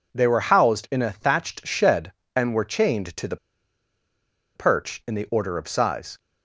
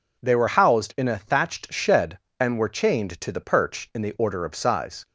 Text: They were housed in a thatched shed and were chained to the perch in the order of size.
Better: second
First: pauses between "the" and "perch"; at 3.3 s; 1.1 s long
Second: none

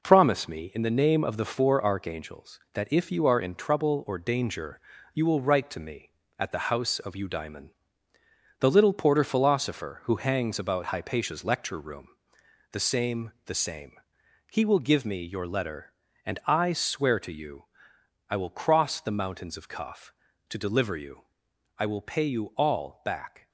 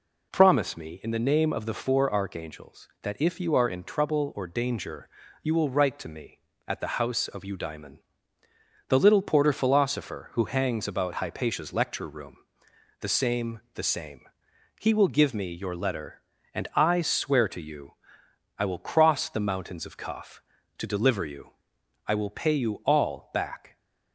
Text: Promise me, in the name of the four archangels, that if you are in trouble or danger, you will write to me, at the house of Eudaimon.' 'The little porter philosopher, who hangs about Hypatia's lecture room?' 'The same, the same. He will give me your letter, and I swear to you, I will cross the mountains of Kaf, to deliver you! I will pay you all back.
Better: second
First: gets quieter; noticeable; throughout; 5 dB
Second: none

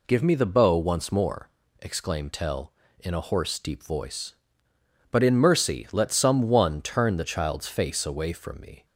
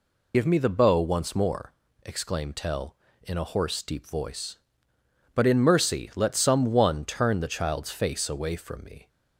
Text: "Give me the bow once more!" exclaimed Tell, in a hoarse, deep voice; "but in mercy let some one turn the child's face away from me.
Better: first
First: none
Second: loses the start of "Give"; at 0.3 s; 45 ms

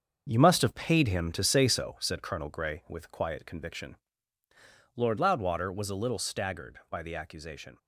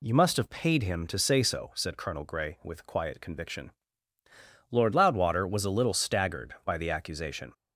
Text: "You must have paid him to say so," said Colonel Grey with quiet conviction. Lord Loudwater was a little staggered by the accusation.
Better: second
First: gets quieter; strong; throughout; 8 dB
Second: none

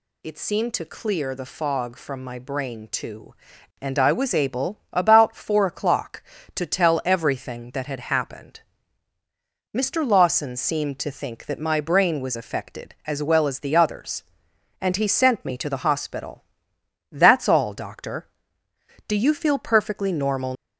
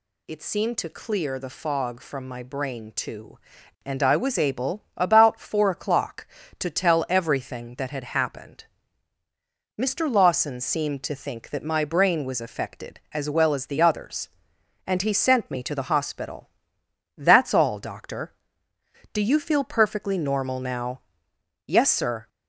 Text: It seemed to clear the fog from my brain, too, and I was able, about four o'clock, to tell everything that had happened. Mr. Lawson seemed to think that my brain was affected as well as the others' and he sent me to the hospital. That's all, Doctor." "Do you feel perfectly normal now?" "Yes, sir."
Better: second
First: stops before "now Yes sir"; at 20.5 s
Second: none

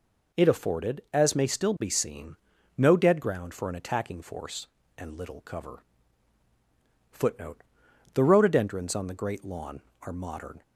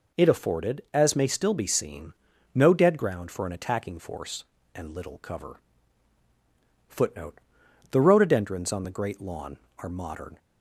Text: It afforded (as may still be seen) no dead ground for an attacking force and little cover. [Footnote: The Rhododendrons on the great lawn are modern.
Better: neither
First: none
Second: none

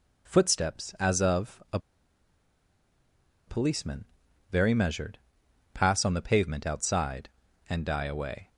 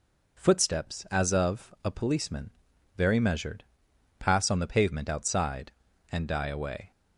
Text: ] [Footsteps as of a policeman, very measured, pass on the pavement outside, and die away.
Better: second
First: pauses between "a" and "policeman"; strong; at 1.7 s; 1.6 s long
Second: none

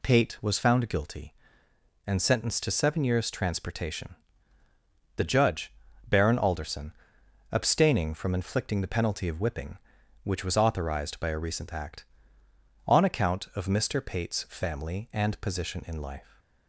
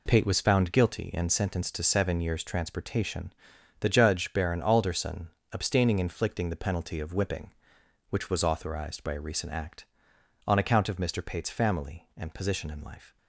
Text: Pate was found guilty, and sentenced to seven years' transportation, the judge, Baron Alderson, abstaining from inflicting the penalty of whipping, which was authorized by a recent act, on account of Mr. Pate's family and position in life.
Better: first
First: none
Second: skips "from"; at 5.9 s

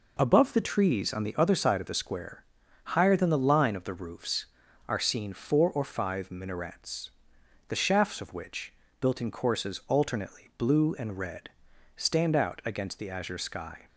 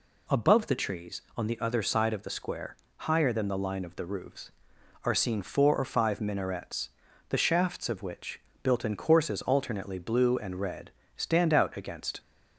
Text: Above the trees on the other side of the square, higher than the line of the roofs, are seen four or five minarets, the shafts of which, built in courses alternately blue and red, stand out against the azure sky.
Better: first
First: none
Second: stops before "the azure sky"; at 12.1 s

